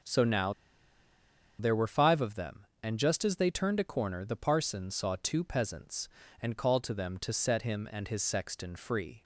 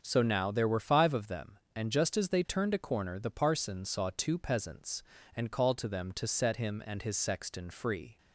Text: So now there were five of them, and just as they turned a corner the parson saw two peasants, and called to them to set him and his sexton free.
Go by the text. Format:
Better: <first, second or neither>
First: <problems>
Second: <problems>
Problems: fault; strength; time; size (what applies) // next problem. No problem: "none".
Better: second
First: starts louder than the rest; until 2.1 s; 7 dB // pauses between "now" and "there"; at 0.5 s; 1.0 s long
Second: starts louder than the rest; until 1.0 s; 6.5 dB